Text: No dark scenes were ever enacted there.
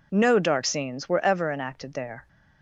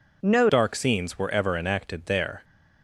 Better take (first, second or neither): first